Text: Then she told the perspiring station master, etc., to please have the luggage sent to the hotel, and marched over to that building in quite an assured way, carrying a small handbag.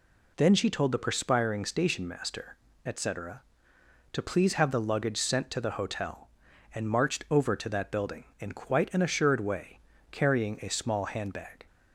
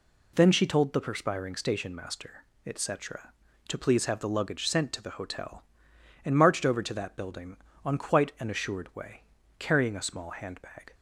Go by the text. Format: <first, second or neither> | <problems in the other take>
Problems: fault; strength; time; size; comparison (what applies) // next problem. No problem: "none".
first | says "on" for "in"; at 7.8 s